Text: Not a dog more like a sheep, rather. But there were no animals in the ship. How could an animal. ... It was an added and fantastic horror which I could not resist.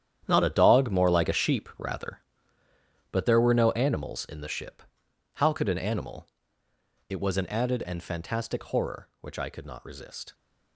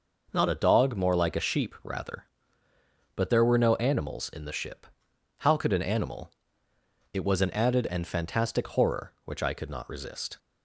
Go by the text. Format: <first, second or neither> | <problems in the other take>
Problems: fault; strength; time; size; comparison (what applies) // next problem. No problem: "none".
second | gets quieter; strong; throughout; 13.5 dB